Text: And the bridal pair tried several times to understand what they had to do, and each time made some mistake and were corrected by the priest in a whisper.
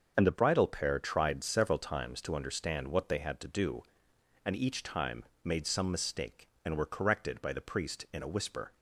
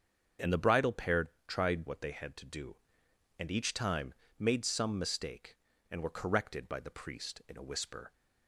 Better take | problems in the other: first | starts louder than the rest; until 1.6 s; 7 dB; also in the first // pauses between "pair" and "tried"; slight; at 1.2 s; 0.20 s long // skips "several times to understand"; at 1.8 s // pauses between "time" and "made"; slight; at 4.1 s; 0.26 s long; slight in the first

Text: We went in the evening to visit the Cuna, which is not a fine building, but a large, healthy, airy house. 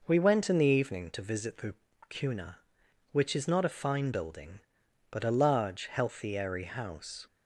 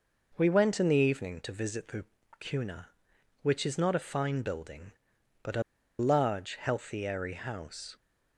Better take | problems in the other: first | pauses between "the" and "Cuna"; slight; at 2.0 s; 0.34 s long; slight in the first // pauses between "a" and "large"; at 5.6 s; 0.36 s long

